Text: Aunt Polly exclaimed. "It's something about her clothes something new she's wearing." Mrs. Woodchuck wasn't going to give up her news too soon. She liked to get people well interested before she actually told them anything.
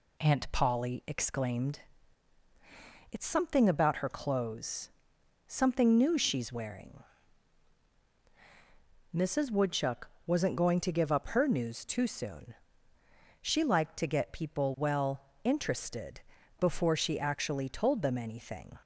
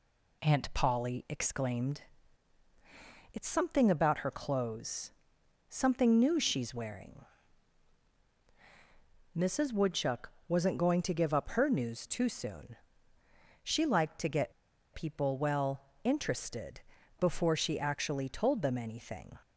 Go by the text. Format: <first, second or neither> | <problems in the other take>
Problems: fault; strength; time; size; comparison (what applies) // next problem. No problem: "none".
first | pauses between "clothes" and "something"; noticeable; at 5.1 s; 0.56 s long; noticeable in the first // pauses between "Woodchuck" and "wasn't"; slight; at 10.3 s; 0.16 s long; slight in the first // pauses between "get" and "people"; at 14.5 s; 0.41 s long // pauses between "well" and "interested"; slight; at 15.8 s; 0.24 s long; slight in the first // pauses between "interested" and "before"; at 16.8 s; 0.40 s long; also in the first